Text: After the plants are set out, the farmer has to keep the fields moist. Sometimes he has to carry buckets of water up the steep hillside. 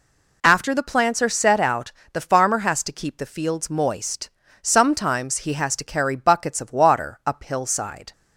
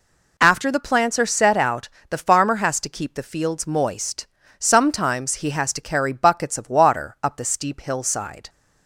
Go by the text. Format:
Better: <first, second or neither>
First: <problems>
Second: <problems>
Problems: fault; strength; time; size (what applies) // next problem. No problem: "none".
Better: second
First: skips "the steep"; at 7.4 s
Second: none